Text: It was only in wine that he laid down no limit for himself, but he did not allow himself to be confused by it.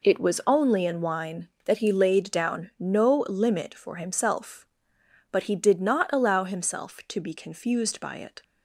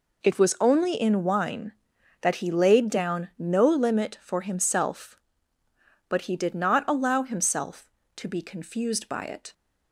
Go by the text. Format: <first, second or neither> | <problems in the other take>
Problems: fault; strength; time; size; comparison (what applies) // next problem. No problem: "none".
neither | none